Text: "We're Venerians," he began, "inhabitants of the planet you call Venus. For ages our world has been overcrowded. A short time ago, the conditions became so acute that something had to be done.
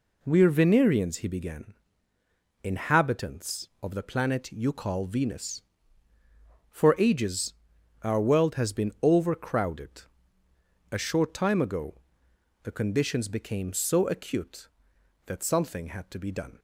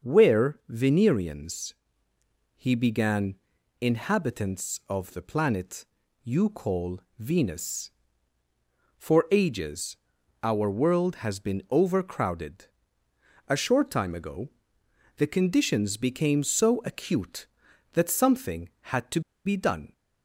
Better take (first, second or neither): first